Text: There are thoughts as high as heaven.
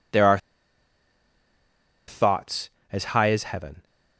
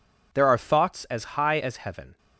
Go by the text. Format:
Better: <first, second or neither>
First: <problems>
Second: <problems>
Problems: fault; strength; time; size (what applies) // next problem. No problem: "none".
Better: second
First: pauses between "are" and "thoughts"; strong; at 0.3 s; 1.7 s long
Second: none